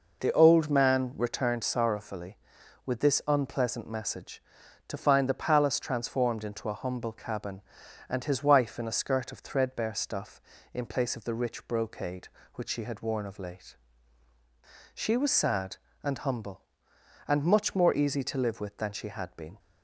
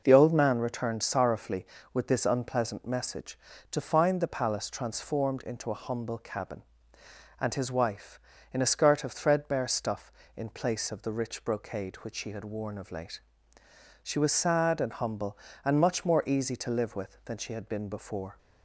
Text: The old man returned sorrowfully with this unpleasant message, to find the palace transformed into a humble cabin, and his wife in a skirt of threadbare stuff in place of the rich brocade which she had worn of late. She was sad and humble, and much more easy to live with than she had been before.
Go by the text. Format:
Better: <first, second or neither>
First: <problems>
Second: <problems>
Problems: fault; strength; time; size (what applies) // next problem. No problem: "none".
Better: second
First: stops before "before"; at 19.5 s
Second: none